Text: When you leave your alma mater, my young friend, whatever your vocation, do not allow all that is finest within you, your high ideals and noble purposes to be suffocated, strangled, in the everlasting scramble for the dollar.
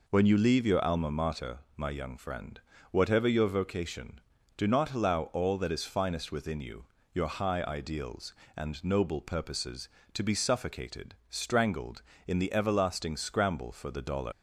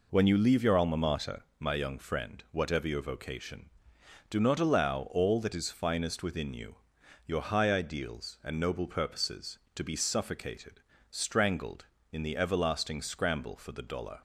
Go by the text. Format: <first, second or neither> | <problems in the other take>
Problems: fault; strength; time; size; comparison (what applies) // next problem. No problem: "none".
second | leaves "dollar" unfinished; at 14.3 s; 100 ms